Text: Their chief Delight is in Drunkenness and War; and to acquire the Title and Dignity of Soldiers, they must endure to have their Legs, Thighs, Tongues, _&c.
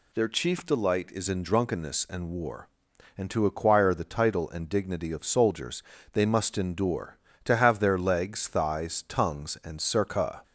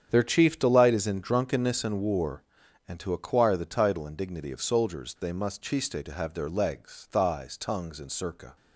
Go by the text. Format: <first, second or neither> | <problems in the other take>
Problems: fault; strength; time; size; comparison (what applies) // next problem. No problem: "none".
first | starts louder than the rest; strong; until 1.1 s; 8.5 dB // says "chiste" for "endure"; at 5.6 s